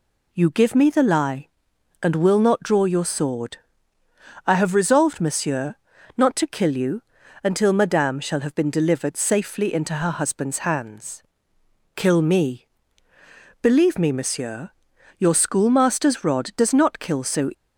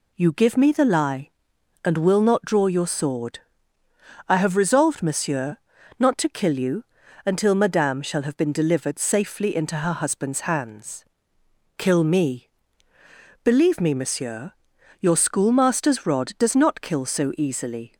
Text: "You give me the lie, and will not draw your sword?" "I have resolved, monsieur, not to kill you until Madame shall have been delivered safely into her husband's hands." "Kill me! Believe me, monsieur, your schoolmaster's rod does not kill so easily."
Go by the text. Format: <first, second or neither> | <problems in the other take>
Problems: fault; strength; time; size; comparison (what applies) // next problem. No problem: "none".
second | pauses between "you" and "until"; at 7.0 s; 0.42 s long; also in the second // stops before "easily"; at 17.5 s